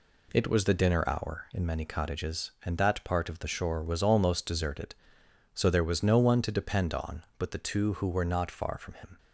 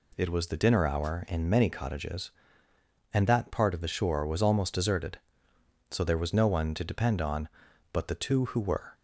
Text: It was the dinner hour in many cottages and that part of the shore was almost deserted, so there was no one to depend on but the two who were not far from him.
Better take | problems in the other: first | stops before "not far from him"; at 8.9 s

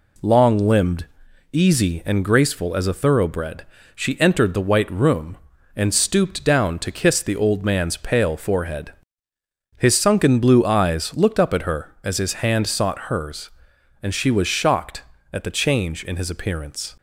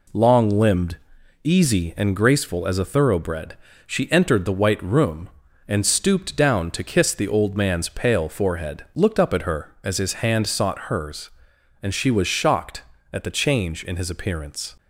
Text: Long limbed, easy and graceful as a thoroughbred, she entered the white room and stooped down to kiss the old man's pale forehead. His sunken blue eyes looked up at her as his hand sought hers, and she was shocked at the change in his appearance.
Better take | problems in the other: first | skips "His sunken blue eyes"; at 8.8 s

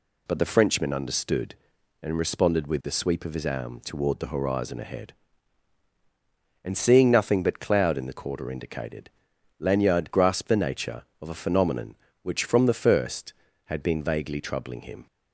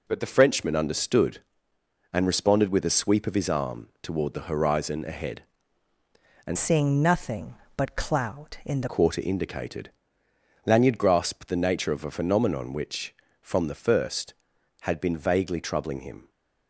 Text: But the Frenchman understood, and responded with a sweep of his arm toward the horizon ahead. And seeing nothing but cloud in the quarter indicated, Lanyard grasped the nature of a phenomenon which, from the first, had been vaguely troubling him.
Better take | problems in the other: first | changes voice from "seeing" to "the"; from 6.5 to 8.8 s; 2.3 s long

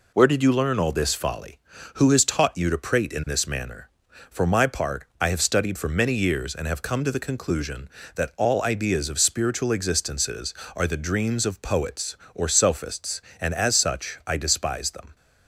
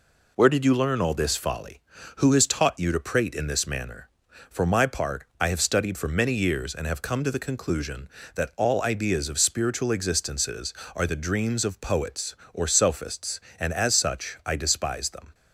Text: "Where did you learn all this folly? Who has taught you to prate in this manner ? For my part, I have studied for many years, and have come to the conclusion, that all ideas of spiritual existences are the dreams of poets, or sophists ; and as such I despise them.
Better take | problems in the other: neither | none

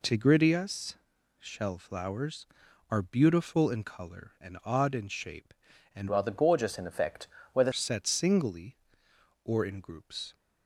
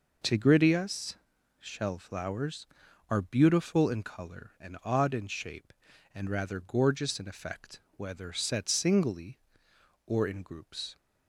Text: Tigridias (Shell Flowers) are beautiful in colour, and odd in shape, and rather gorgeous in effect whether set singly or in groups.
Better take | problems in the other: second | changes voice from "rather" to "whether"; from 6.0 to 7.7 s; 1.7 s long // pauses between "effect" and "whether"; slight; at 7.2 s; 0.26 s long; slight in the second

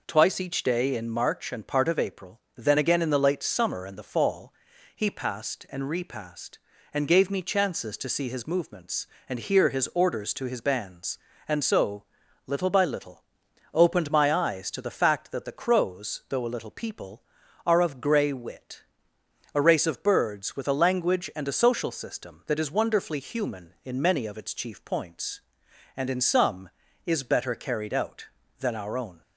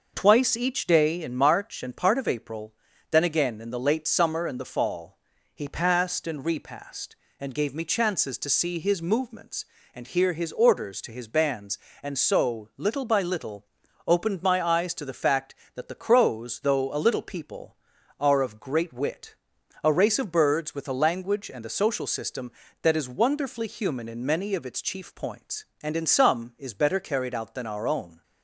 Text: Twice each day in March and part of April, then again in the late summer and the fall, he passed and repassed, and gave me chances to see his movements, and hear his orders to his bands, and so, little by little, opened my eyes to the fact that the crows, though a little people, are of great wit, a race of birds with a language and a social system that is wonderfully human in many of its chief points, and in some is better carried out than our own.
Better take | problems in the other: second | says "grey" for "great"; at 18.0 s

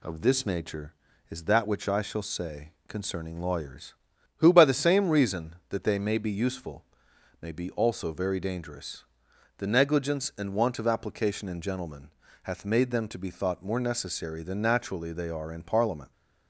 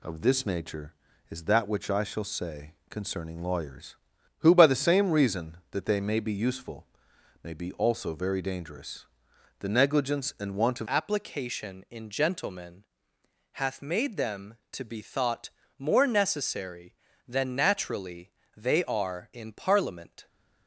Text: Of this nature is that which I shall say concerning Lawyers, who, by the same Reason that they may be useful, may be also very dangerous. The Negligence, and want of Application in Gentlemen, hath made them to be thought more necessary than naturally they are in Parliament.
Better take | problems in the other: first | pauses between "say" and "concerning"; slight; at 2.7 s; 0.16 s long; slight in the first // changes voice at "Application"; from 10.8 s on; 9.4 s long // pauses between "thought" and "more"; slight; at 15.5 s; 0.28 s long // pauses between "naturally" and "they"; slight; at 18.3 s; 0.24 s long

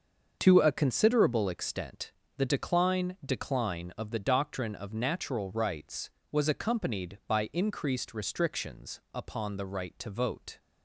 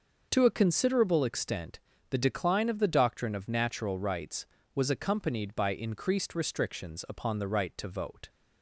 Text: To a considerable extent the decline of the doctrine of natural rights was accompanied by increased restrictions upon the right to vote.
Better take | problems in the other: second | starts louder than the rest; until 1.4 s; 6.5 dB; noticeable in the second // pauses between "extent" and "the"; slight; at 2.1 s; 0.24 s long; slight in the second // says "decline" twice; at 3.2 s // pauses between "restrictions" and "upon"; slight; at 8.9 s; 0.16 s long

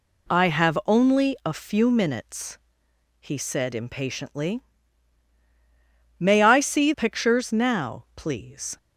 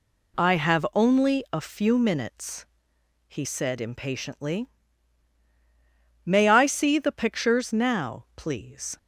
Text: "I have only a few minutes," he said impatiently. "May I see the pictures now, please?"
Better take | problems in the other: second | skips "the"; at 6.9 s

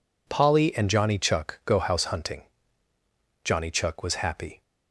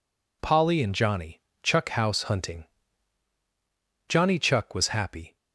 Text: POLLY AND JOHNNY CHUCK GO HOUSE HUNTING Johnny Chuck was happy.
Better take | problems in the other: first | pauses between "JOHNNY" and "CHUCK"; slight; at 1.4 s; 0.22 s long // skips "GO"; at 1.8 s // pauses between "HUNTING" and "Johnny"; strong; at 2.6 s; 1.4 s long; also in the first

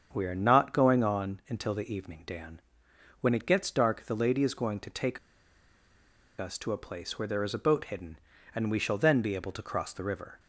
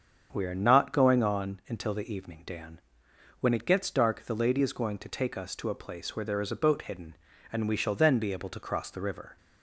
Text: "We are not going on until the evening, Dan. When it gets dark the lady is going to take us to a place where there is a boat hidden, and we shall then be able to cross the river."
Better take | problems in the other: second | starts louder than the rest; strong; until 1.1 s; 7.5 dB; strong in the second // pauses between "take" and "us"; at 5.1 s; 1.2 s long

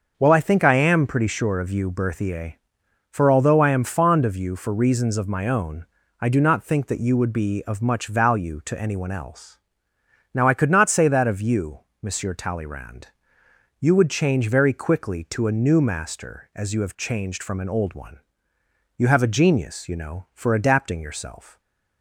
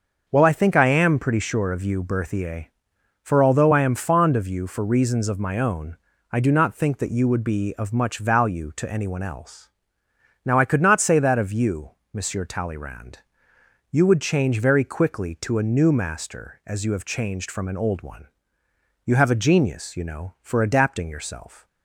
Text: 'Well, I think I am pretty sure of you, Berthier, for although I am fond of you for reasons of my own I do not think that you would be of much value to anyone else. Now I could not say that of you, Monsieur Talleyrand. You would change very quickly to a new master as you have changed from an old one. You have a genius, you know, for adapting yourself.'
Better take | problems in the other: neither | starts louder than the rest; the same in both // pauses between "own" and "I"; slight; the same in both

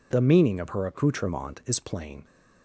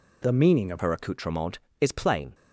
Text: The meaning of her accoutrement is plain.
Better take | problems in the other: first | changes voice at "her"; from 0.7 s on; 1.6 s long

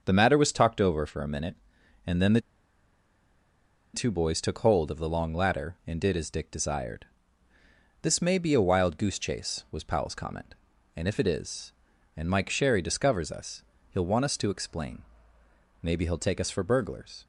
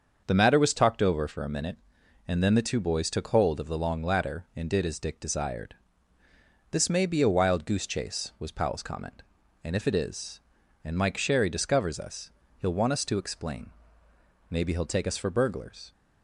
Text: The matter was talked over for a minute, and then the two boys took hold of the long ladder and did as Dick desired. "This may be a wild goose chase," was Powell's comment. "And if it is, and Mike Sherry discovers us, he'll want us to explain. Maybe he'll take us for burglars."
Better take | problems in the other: second | starts louder than the rest; until 1.0 s; 6.5 dB; also in the second // pauses between "the" and "two"; strong; at 2.3 s; 1.5 s long

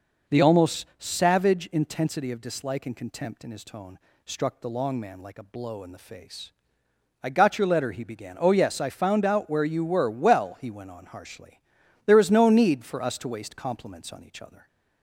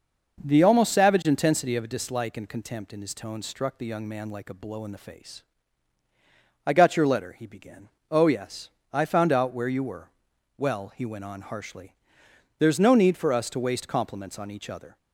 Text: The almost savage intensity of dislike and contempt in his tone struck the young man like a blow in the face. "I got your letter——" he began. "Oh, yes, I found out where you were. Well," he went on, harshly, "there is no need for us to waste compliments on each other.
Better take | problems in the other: second | pauses between "tone" and "struck"; slight; at 3.9 s; 0.26 s long // says "long" for "young"; at 4.7 s

